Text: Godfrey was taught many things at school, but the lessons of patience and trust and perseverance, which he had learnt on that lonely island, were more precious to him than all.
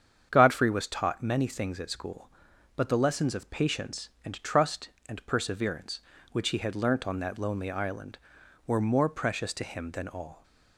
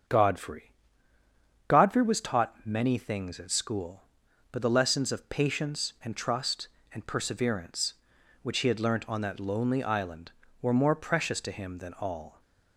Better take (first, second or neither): first